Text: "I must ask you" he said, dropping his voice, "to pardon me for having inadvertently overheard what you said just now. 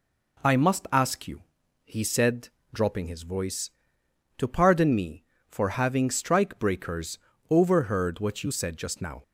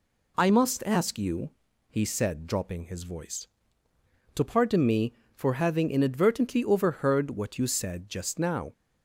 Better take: second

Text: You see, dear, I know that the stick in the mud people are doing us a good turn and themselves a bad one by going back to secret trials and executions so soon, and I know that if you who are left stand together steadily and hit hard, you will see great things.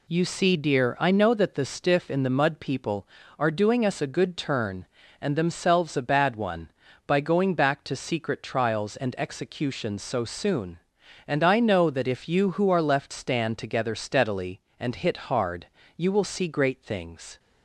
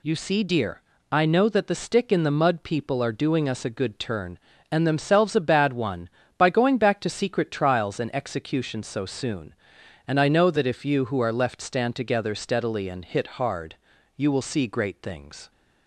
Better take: second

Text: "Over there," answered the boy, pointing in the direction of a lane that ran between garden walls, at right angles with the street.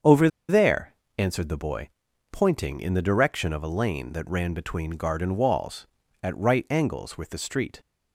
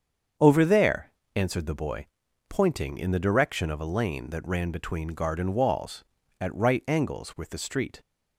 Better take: second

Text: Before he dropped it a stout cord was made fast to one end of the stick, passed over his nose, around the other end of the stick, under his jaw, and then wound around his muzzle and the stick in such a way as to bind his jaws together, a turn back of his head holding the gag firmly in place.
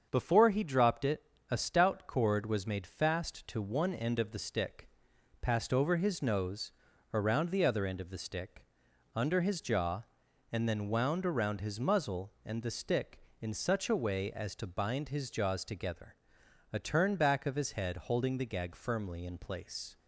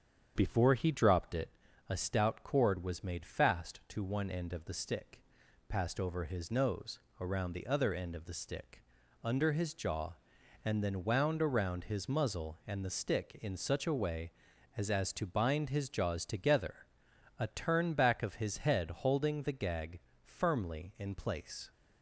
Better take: first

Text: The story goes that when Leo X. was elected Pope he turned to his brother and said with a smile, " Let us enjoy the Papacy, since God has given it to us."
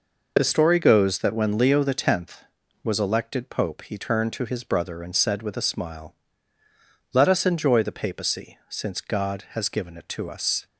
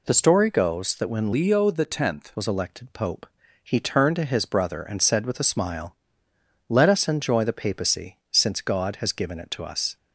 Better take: first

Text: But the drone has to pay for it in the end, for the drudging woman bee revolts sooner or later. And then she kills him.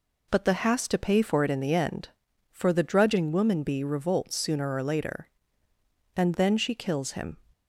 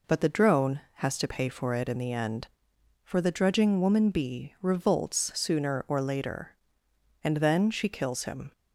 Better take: second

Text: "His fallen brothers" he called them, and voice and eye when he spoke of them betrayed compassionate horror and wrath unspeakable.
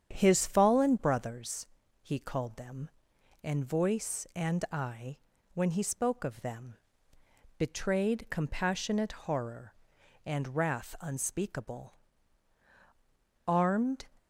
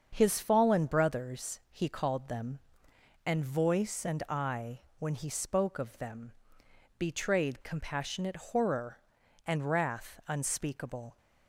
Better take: second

